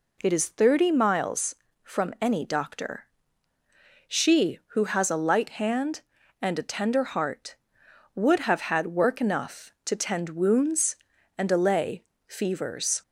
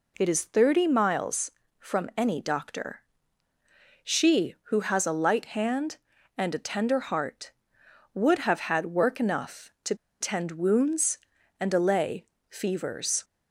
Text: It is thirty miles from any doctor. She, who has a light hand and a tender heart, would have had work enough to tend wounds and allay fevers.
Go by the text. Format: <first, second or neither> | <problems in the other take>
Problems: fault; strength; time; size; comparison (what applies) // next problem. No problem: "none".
first | pauses between "to" and "tend"; slight; at 9.9 s; 0.25 s long // pauses between "allay" and "fevers"; slight; at 12.2 s; 0.24 s long; slight in the first